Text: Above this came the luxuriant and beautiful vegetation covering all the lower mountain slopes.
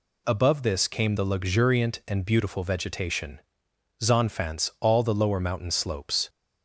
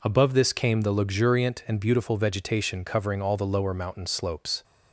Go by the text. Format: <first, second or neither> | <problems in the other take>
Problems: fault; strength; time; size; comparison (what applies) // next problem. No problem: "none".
second | says "zonfants" for "covering"; at 4.0 s